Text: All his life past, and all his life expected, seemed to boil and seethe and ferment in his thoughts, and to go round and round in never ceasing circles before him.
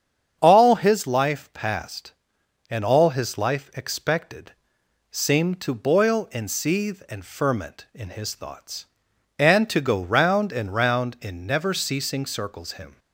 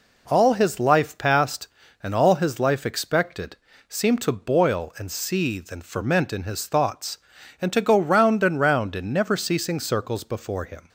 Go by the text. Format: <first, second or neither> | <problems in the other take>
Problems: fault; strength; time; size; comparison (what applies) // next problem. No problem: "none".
second | starts louder than the rest; strong; until 1.4 s; 7 dB // skips "before"; at 12.7 s